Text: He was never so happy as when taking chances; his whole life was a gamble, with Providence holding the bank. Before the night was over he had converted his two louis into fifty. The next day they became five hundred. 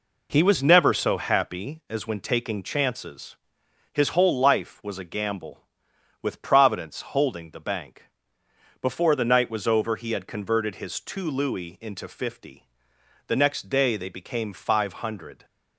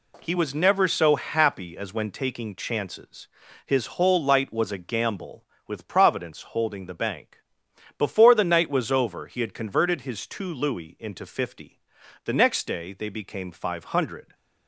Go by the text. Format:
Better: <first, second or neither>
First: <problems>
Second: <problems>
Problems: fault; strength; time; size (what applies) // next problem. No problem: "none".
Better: first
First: none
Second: says "light" for "life"; at 4.2 s